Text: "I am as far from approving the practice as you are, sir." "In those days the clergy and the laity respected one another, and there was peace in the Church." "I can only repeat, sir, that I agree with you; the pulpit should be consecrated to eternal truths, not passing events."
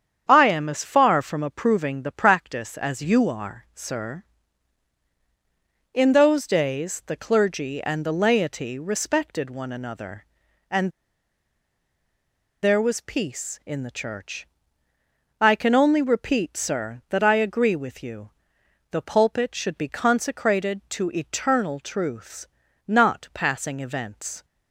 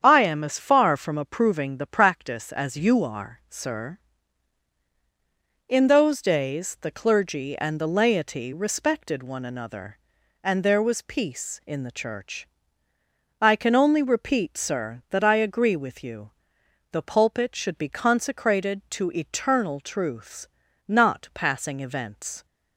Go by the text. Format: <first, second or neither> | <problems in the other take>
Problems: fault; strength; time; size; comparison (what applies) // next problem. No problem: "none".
second | starts louder than the rest; strong; until 1.2 s; 8 dB; strong in the second // pauses between "and" and "there"; strong; at 10.9 s; 1.7 s long